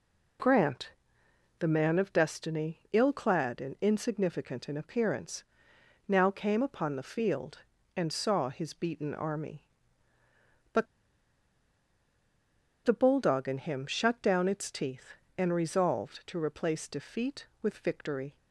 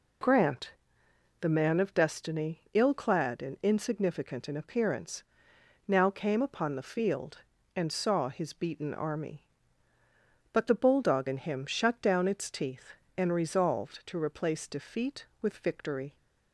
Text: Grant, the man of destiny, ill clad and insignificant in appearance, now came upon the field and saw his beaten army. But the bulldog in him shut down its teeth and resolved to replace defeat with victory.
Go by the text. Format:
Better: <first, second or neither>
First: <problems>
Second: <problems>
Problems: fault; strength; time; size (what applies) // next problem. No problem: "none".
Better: second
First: pauses between "But" and "the"; strong; at 10.8 s; 1.9 s long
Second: none